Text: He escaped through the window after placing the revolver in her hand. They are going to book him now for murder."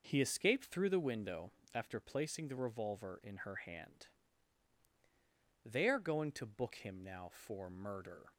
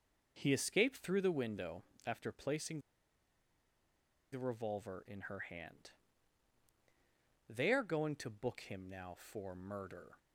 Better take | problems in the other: first | pauses between "window" and "after"; slight; at 1.8 s; 0.24 s long; slight in the first // pauses between "placing" and "the"; strong; at 2.7 s; 1.5 s long

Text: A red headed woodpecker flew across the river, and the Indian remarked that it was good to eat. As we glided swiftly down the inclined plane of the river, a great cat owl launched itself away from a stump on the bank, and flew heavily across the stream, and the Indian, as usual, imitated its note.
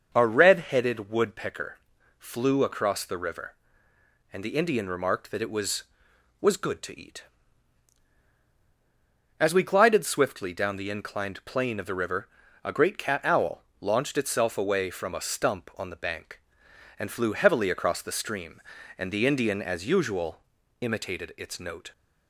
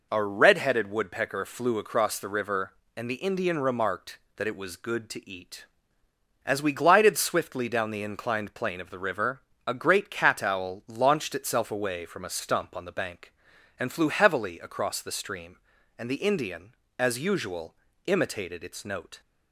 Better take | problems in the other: second | starts louder than the rest; until 1.1 s; 6 dB // pauses between "woodpecker" and "flew"; at 1.7 s; 0.40 s long // says "was" twice; at 6.3 s // pauses between "owl" and "launched"; slight; at 13.6 s; 0.18 s long

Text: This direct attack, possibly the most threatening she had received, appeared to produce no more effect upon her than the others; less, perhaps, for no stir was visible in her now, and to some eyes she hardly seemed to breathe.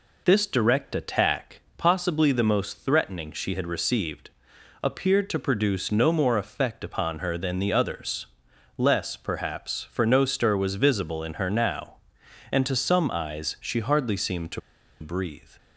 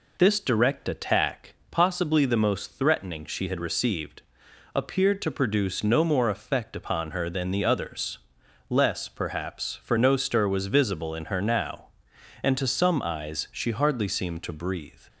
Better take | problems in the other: second | pauses between "to" and "breathe"; at 14.5 s; 0.40 s long

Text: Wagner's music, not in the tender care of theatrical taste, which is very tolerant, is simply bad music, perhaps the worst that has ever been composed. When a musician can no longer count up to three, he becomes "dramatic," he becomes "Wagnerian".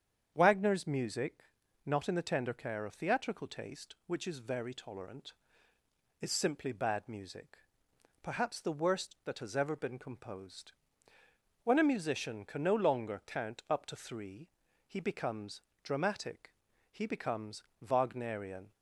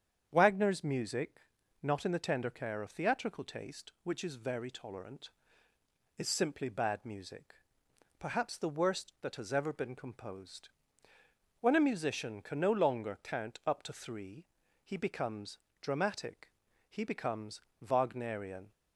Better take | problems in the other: neither | starts louder than the rest; strong; the same in both // pauses between "becomes" and "dramatic"; slight; the same in both // pauses between "becomes" and "Wagnerian"; slight; the same in both

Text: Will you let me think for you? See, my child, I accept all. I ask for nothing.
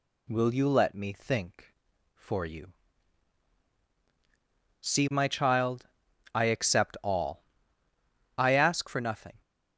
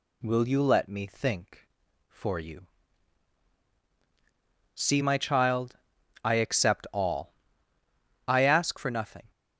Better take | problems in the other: neither | none

